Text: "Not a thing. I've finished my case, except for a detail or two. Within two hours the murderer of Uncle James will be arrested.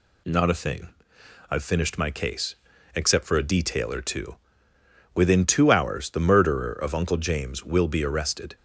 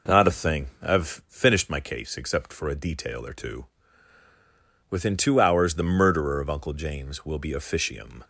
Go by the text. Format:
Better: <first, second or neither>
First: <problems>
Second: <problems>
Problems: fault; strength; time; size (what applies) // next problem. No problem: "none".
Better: first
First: none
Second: says "officium" for "arrested"; at 7.5 s